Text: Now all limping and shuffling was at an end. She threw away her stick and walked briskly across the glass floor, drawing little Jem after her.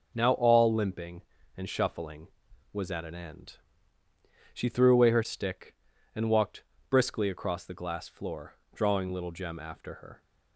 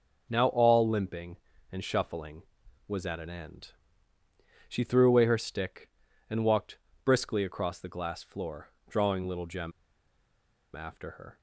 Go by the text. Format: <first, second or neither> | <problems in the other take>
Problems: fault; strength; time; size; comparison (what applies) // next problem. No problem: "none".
first | pauses between "walked" and "briskly"; slight; at 6.7 s; 0.26 s long; slight in the first // pauses between "Jem" and "after"; at 9.7 s; 1.0 s long